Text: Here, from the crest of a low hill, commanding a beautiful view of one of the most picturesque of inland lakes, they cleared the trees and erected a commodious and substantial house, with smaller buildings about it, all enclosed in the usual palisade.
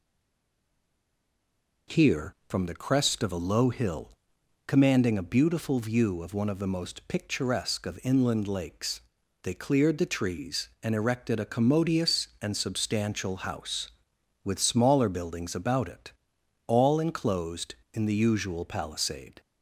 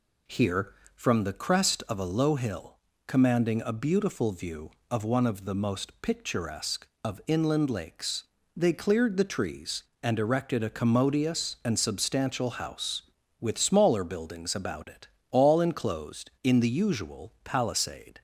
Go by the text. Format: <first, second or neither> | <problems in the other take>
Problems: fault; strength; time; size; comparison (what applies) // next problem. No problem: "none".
second | stays silent before the first word; noticeable; until 1.8 s; 1.8 s long